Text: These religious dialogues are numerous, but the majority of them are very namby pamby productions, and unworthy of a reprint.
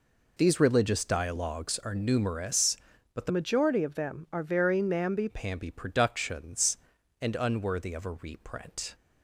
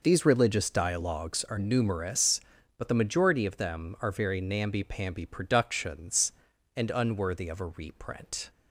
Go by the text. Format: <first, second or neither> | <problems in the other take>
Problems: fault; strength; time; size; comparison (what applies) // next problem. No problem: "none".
second | changes voice from "majority" to "namby"; from 3.2 to 5.2 s; 2.0 s long